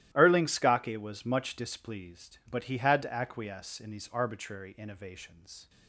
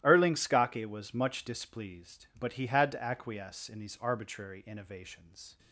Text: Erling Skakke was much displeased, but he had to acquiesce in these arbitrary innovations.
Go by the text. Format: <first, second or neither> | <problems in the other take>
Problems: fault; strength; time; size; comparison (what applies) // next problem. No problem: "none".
neither | starts louder than the rest; strong; the same in both